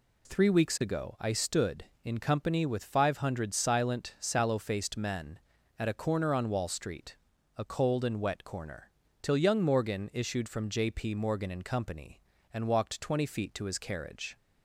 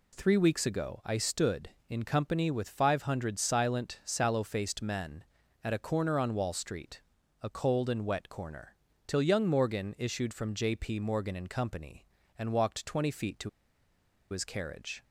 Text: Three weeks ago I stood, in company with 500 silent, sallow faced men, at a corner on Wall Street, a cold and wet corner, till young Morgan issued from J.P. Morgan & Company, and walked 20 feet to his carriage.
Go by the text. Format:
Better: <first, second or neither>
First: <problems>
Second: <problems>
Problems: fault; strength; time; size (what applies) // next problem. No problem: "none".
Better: first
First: none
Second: pauses between "to" and "his"; noticeable; at 13.4 s; 0.81 s long